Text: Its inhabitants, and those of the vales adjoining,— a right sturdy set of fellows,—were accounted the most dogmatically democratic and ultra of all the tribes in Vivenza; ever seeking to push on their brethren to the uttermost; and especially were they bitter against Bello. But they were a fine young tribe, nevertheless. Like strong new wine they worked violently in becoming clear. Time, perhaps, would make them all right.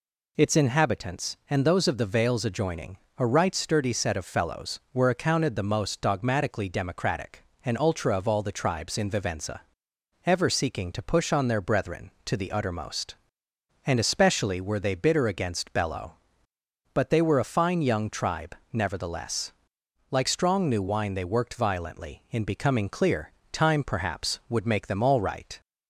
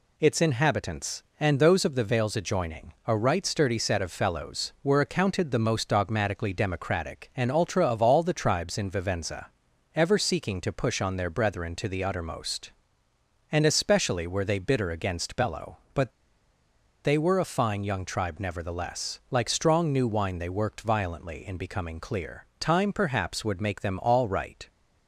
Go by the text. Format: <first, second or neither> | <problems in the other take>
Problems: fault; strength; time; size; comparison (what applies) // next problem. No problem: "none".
first | pauses between "But" and "they"; noticeable; at 16.1 s; 0.94 s long